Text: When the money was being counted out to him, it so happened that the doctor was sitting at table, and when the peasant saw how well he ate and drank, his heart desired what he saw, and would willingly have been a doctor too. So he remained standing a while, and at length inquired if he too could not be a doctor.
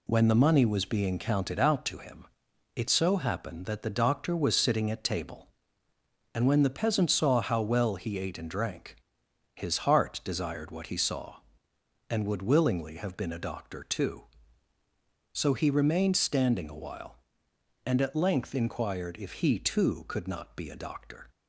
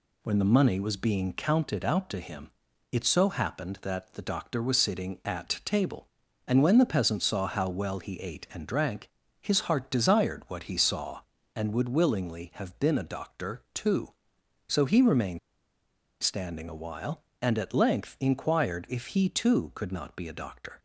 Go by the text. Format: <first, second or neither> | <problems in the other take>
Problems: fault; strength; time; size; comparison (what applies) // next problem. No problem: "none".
first | pauses between "remained" and "standing"; noticeable; at 15.3 s; 0.83 s long